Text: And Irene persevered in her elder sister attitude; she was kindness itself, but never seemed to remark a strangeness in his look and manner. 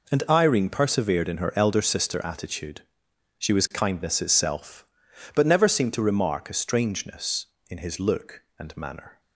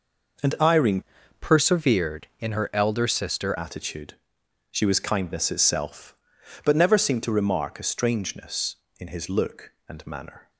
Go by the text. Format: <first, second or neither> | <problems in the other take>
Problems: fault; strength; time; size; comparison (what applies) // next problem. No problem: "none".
first | changes voice from "persevered" to "sister"; from 1.3 to 3.5 s; 2.2 s long